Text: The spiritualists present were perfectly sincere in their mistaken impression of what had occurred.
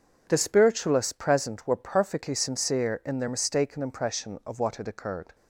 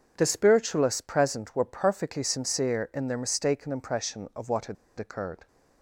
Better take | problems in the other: first | pauses between "had" and "occurred"; slight; at 4.7 s; 0.23 s long

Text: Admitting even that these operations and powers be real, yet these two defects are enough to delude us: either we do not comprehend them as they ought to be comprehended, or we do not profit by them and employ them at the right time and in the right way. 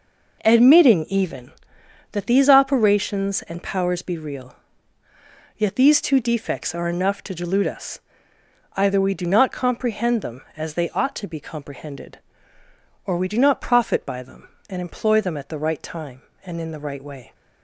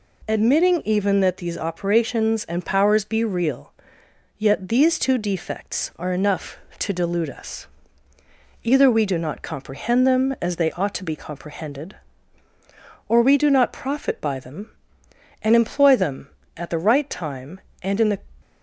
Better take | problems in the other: first | stops before "right way"; at 18.4 s

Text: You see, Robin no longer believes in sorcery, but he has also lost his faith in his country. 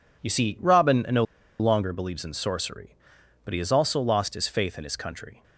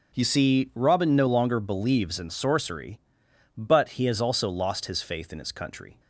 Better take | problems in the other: second | pauses between "no" and "longer"; at 1.2 s; 0.37 s long

